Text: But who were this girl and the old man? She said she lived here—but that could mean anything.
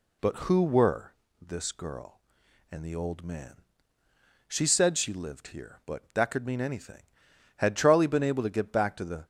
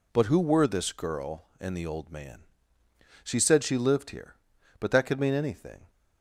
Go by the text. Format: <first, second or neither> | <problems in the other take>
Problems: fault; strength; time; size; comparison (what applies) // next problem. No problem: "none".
second | pauses between "were" and "this"; slight; at 1.1 s; 0.28 s long // goes on to say "Had Charlie been able to get back to the"; strong; from 7.5 s on; 1.6 s long